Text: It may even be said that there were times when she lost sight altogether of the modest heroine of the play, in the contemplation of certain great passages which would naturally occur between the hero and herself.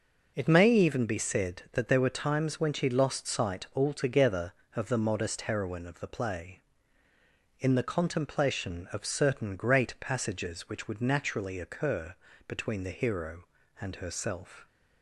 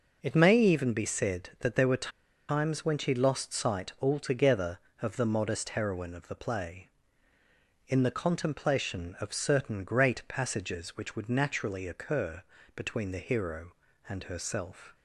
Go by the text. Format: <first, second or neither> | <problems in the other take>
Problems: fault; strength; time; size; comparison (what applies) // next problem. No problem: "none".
first | pauses between "were" and "times"; at 2.1 s; 0.39 s long // pauses between "occur" and "between"; slight; at 12.4 s; 0.34 s long; slight in the first